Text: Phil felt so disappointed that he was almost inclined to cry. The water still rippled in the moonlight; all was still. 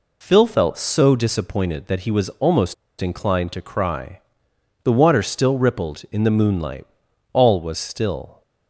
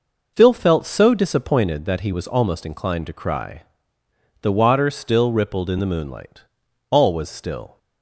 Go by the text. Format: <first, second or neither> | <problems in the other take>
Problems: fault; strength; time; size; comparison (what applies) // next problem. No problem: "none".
second | pauses between "almost" and "inclined"; slight; at 2.7 s; 0.26 s long